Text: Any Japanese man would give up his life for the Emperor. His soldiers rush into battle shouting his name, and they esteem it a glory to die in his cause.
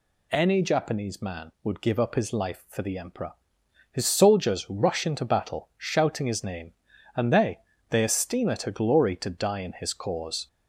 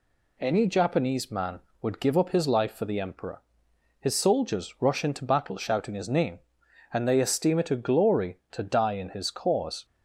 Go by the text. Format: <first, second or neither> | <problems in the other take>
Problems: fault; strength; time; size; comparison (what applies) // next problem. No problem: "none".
second | says "they" twice; at 7.9 s